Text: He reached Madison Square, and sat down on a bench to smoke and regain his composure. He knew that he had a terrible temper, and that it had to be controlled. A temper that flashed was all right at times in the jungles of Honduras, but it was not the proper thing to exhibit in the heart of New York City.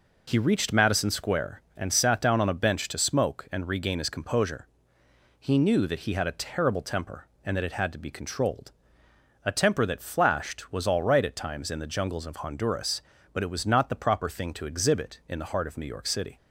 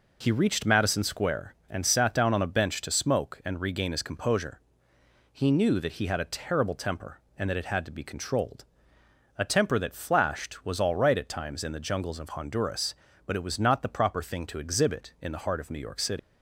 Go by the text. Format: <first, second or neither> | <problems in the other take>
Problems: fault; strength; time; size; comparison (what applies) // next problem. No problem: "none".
first | leaves "City" unfinished; at 16.1 s; 100 ms